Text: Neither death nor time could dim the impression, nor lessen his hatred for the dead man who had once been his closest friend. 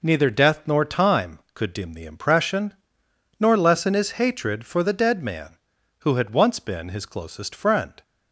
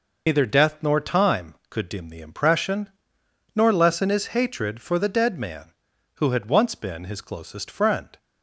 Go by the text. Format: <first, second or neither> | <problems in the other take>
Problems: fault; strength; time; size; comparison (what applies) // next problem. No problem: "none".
first | loses the start of "Neither"; at 0.2 s; 90 ms